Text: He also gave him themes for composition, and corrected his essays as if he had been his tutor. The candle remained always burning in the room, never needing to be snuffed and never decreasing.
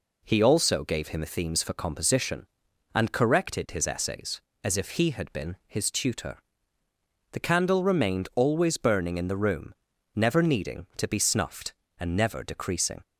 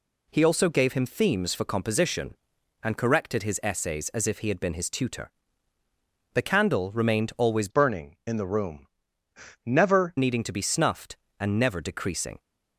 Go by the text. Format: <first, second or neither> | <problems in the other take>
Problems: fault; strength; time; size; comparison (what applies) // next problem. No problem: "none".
first | changes voice from "burning" to "never"; from 7.7 to 10.1 s; 2.4 s long